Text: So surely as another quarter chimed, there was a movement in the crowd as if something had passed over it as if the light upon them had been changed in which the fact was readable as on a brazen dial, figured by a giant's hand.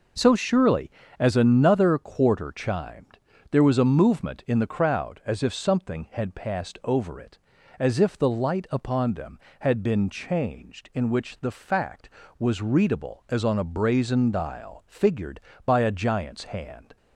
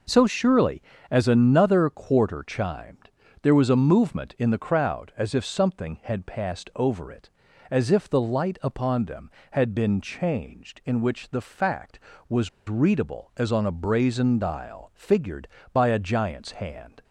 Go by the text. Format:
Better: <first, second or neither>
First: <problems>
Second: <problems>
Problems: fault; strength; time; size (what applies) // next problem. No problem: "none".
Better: first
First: none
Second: pauses between "was" and "readable"; slight; at 12.4 s; 0.18 s long